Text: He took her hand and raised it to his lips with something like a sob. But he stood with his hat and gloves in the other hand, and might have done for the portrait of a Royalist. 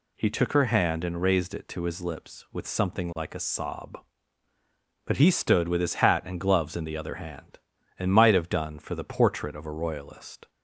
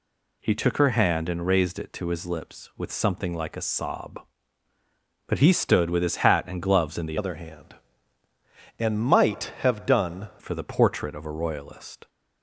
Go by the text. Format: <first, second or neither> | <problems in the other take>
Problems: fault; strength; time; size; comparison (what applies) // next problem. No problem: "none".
first | changes voice from "other" to "done"; from 7.1 to 10.2 s; 3.1 s long